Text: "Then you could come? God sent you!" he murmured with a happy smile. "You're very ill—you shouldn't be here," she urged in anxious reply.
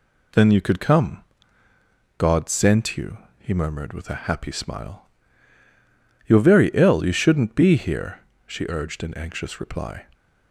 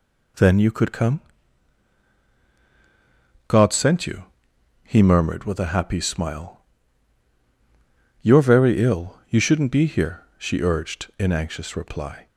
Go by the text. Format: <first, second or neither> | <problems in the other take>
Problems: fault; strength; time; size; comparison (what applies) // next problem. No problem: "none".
neither | none